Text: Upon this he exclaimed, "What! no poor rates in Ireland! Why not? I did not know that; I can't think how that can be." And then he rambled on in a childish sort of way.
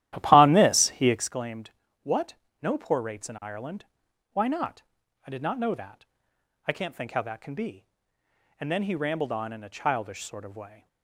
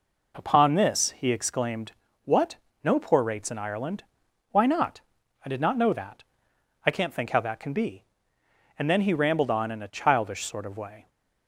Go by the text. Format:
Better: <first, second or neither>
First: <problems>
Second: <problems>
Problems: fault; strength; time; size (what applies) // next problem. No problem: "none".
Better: second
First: starts louder than the rest; strong; until 1.3 s; 13 dB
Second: none